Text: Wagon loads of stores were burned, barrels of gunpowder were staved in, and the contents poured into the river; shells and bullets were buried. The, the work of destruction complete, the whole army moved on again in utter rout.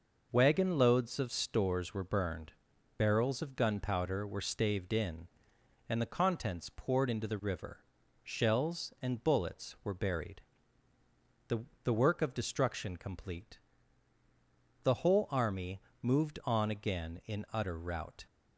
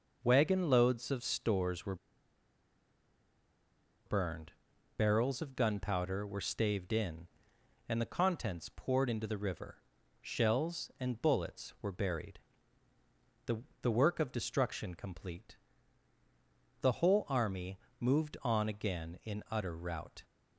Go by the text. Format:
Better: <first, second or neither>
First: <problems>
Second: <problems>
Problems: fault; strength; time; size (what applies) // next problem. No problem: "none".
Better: first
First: pauses between "army" and "moved"; slight; at 15.8 s; 0.22 s long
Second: pauses between "were" and "burned"; strong; at 1.9 s; 2.1 s long // pauses between "army" and "moved"; slight; at 17.7 s; 0.22 s long